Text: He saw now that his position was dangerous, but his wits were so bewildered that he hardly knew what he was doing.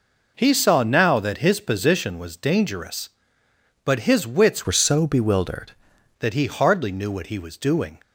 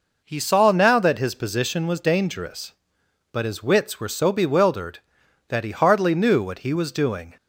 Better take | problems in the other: second | changes voice from "were" to "bewildered"; from 4.6 to 5.7 s; 1.1 s long

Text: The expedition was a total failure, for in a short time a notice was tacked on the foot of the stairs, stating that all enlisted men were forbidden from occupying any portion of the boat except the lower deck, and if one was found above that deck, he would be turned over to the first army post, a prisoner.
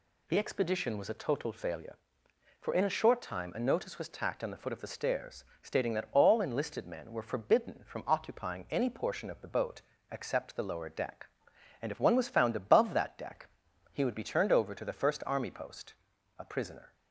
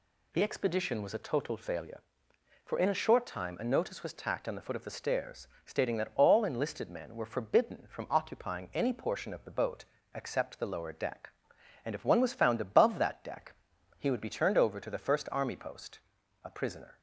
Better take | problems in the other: neither | pauses between "boat" and "except"; slight; the same in both

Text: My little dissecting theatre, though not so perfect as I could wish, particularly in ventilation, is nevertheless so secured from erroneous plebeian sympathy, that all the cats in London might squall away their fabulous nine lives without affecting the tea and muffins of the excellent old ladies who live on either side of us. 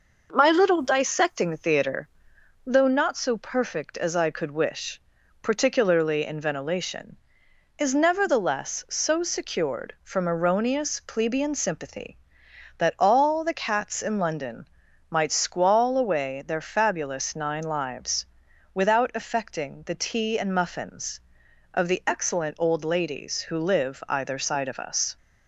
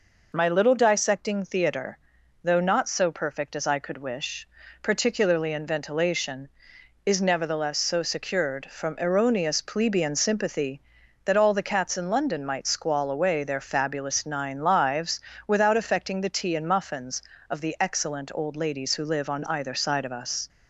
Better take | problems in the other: second | pauses between "London" and "might"; at 14.6 s; 0.42 s long // pauses between "lives" and "without"; noticeable; at 18.2 s; 0.48 s long; slight in the second // skips "on"; at 24.0 s

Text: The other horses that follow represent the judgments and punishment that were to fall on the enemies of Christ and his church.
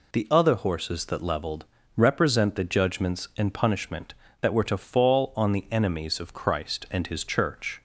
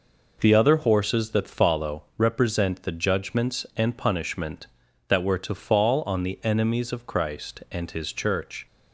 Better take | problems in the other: second | says "leveled" for "follow"; at 1.2 s

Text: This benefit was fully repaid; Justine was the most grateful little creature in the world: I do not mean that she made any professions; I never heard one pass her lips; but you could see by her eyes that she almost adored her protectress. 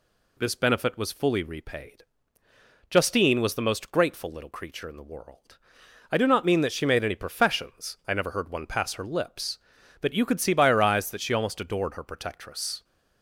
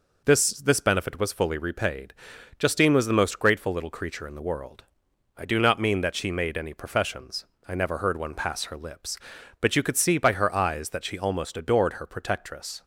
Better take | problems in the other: first | says "This" twice; at 0.5 s

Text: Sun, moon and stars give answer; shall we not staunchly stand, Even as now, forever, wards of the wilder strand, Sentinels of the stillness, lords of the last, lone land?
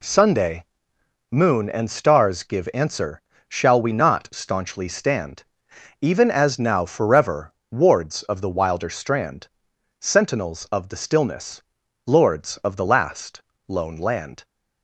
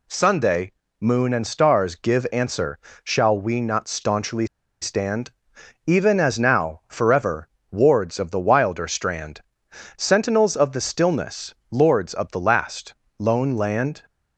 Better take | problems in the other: first | pauses between "staunchly" and "stand"; at 4.4 s; 0.36 s long

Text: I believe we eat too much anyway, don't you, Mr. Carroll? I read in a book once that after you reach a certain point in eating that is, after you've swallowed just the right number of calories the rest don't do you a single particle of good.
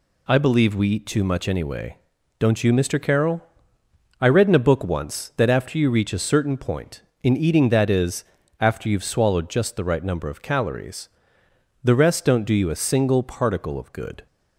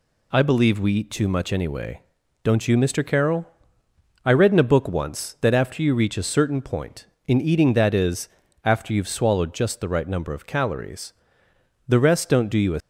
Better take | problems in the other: first | pauses between "calories" and "the"; noticeable; at 11.1 s; 0.74 s long; noticeable in the first // stops before "single particle of good"; at 12.8 s

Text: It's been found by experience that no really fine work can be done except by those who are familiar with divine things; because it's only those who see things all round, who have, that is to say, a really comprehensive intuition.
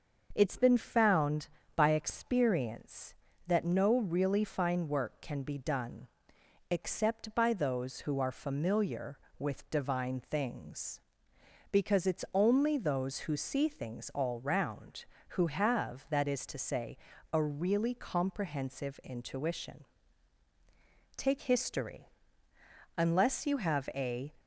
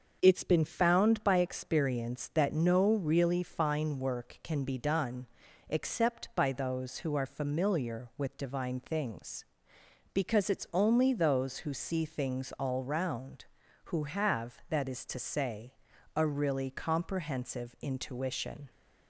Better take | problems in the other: second | starts louder than the rest; until 1.3 s; 6.5 dB; also in the second // pauses between "done" and "except"; noticeable; at 6.0 s; 0.62 s long; also in the second // goes on to say "Take history Unless you have a"; strong; from 21.1 s on; 3.1 s long

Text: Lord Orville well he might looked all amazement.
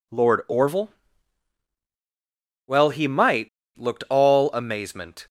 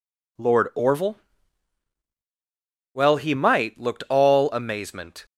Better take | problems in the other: second | pauses between "Orville" and "well"; strong; at 0.9 s; 1.7 s long; strong in the second // pauses between "might" and "looked"; slight; at 3.4 s; 0.29 s long

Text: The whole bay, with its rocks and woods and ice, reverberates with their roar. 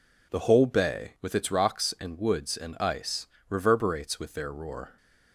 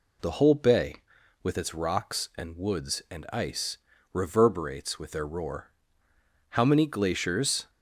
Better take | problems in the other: first | goes on to say "How many glaciers"; noticeable; from 6.4 s on; 1.2 s long

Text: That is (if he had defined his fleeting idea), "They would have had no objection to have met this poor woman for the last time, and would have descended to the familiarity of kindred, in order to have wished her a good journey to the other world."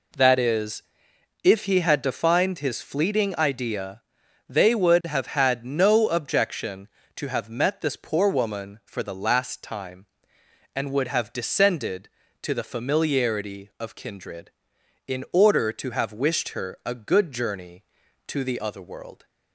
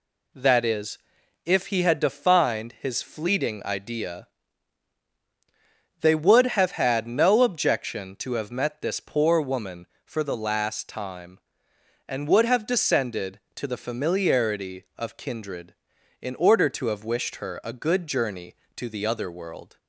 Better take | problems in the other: neither | none

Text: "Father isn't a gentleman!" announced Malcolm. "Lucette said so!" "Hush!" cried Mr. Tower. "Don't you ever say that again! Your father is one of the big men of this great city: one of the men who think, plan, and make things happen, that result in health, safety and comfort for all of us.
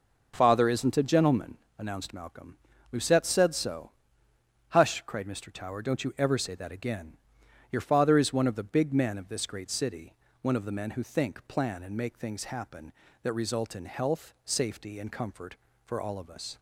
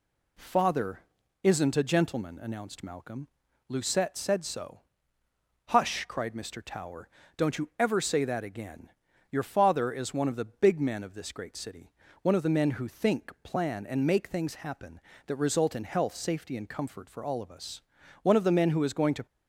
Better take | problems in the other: first | pauses between "Father" and "isn't"; at 0.9 s; 0.42 s long // goes on to say "One of the men who is going to"; noticeable; from 18.2 s on; 1.0 s long

